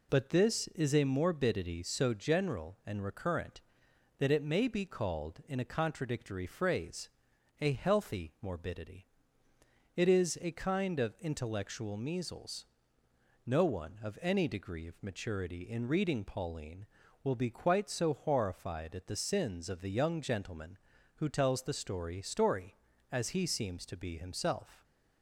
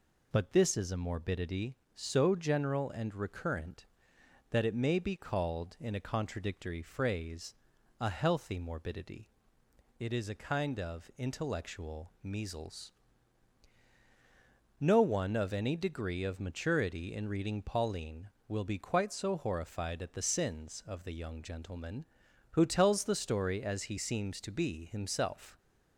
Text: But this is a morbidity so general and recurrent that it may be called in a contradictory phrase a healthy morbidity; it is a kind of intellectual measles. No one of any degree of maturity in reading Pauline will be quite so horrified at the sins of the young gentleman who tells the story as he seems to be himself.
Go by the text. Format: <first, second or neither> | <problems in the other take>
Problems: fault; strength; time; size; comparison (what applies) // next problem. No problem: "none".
second | pauses between "phrase" and "a"; noticeable; at 7.0 s; 0.52 s long; noticeable in the second // says "story" twice; at 22.2 s